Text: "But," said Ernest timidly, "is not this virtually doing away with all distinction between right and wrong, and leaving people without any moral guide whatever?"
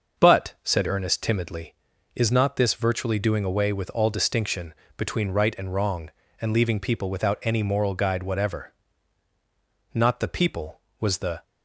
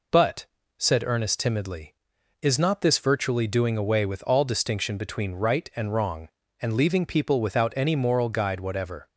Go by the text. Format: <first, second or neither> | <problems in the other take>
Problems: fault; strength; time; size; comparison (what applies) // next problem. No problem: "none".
second | starts louder than the rest; noticeable; until 1.2 s; 6 dB // pauses between "distinction" and "between"; slight; at 4.7 s; 0.24 s long // goes on to say "Not the people was the"; from 9.9 s on; 1.5 s long